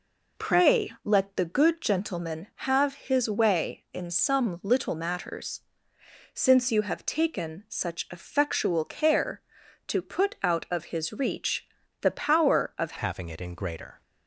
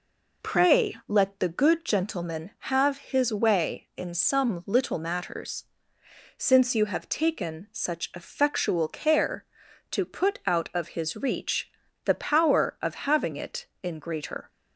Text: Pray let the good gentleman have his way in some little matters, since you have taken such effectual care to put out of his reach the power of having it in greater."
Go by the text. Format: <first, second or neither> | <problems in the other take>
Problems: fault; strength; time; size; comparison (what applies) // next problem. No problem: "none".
second | pauses between "reach" and "the"; slight; at 11.6 s; 0.36 s long; slight in the second // changes voice at "having"; from 12.9 s on; 1.1 s long